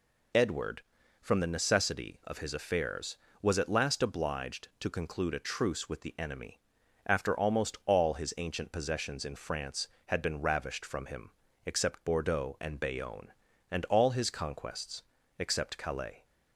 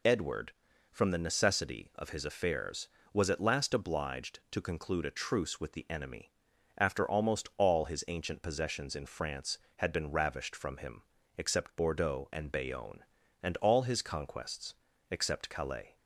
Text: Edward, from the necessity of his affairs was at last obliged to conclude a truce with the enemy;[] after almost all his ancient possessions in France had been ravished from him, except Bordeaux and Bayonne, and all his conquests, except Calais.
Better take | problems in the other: neither | none

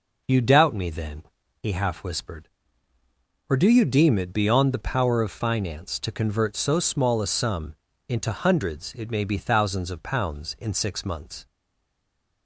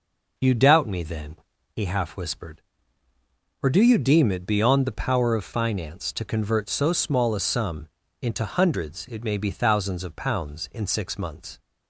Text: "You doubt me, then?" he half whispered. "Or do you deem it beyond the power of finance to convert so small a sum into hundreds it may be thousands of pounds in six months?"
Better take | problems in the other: second | pauses between "sum" and "into"; slight; at 7.7 s; 0.32 s long; slight in the second // stays silent after the last word; from 11.4 s on; 1.0 s long

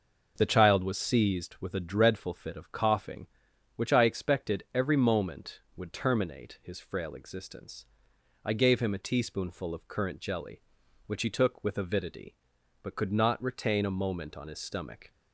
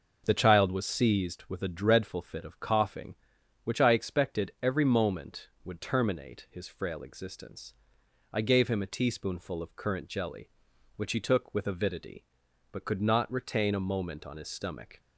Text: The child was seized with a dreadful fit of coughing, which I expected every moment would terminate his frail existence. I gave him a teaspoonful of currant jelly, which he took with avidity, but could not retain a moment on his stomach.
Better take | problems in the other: neither | none

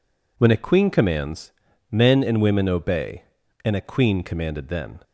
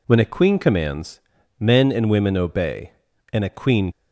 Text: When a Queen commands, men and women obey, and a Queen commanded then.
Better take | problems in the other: first | stops before "commanded then"; at 3.9 s

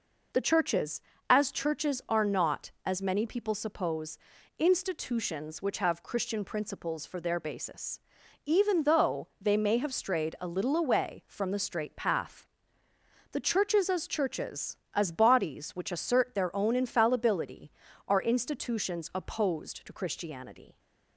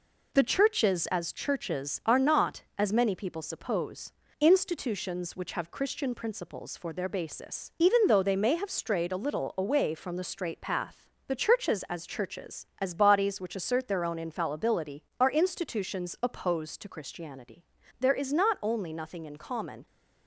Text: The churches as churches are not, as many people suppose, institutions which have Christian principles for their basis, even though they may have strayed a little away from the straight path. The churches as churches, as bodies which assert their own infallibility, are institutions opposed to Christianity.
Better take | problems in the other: first | goes on to say "There is not only nothing in common"; strong; from 17.9 s on; 1.8 s long

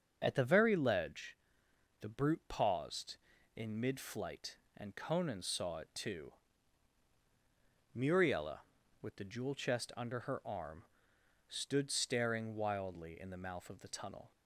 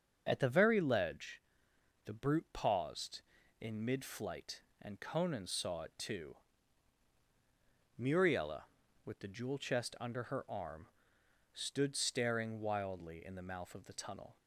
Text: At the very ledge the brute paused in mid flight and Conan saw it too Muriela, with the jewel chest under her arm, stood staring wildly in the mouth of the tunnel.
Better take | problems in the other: neither | starts louder than the rest; the same in both // pauses between "ledge" and "the"; noticeable; the same in both // pauses between "too" and "Muriela"; strong; the same in both

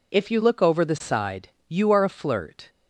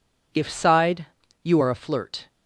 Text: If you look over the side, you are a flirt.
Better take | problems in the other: first | skips "you look over the"; at 0.4 s

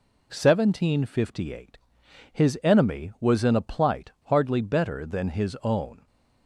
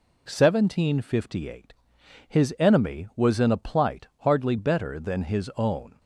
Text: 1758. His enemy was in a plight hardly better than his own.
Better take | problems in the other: neither | none

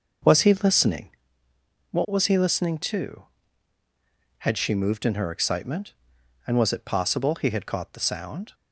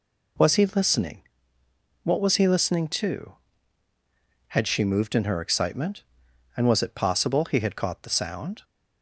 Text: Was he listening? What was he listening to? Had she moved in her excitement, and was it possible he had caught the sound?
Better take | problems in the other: second | starts louder than the rest; noticeable; until 1.3 s; 6 dB

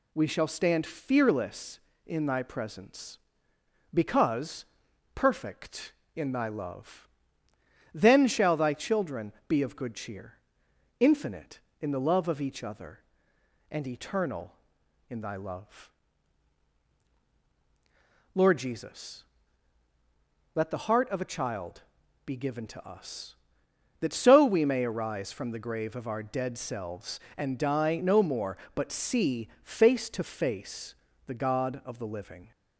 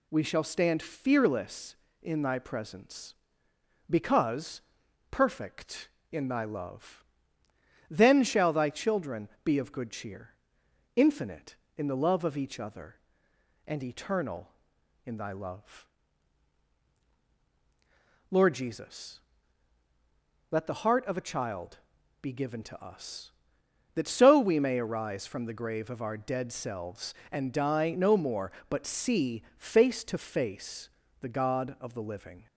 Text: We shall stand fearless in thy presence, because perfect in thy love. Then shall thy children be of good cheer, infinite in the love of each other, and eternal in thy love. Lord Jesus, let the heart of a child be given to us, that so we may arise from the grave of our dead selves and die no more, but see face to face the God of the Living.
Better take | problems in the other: neither | pauses between "because" and "perfect"; noticeable; the same in both // pauses between "children" and "be"; slight; the same in both // pauses between "child" and "be"; the same in both // pauses between "face" and "the"; slight; the same in both

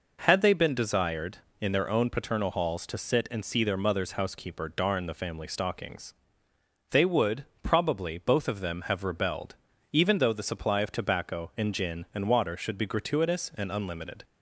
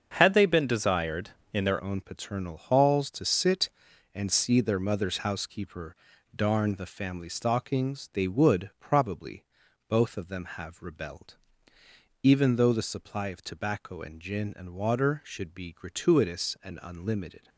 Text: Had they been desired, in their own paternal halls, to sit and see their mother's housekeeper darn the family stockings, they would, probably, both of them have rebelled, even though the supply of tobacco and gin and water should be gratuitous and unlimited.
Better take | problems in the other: first | starts louder than the rest; until 1.1 s; 7 dB // changes voice at "own"; from 1.8 s on; 15.6 s long // pauses between "housekeeper" and "darn"; at 5.9 s; 0.40 s long

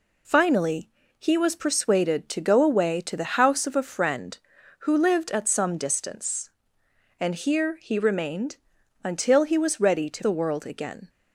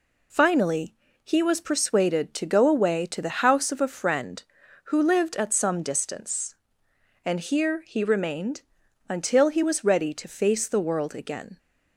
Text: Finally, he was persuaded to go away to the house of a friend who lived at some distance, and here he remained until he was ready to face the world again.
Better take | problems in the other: second | pauses between "remained" and "until"; noticeable; at 8.5 s; 0.48 s long; noticeable in the second // skips "face"; at 10.2 s

